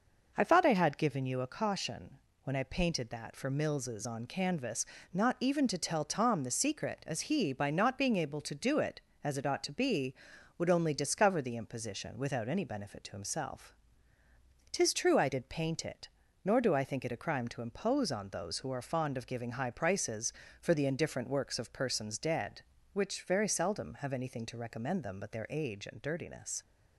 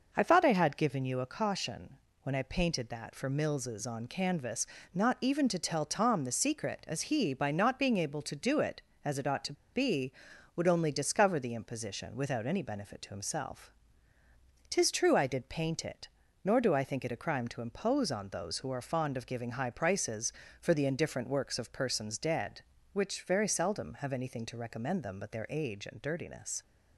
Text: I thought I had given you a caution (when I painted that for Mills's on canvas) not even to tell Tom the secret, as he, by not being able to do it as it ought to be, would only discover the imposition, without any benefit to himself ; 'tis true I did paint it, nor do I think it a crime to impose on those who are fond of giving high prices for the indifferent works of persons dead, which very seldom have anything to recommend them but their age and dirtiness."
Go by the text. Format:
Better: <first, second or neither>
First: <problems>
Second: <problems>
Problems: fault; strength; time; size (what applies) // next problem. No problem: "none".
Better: first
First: none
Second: pauses between "to" and "be"; slight; at 9.5 s; 0.18 s long